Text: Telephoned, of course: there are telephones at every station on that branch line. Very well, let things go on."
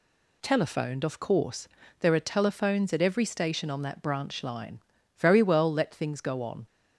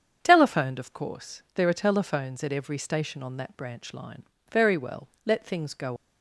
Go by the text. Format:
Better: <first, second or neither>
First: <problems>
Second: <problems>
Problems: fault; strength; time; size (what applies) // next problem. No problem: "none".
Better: first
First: none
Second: starts louder than the rest; strong; until 1.2 s; 7.5 dB // stops before "on"; at 5.9 s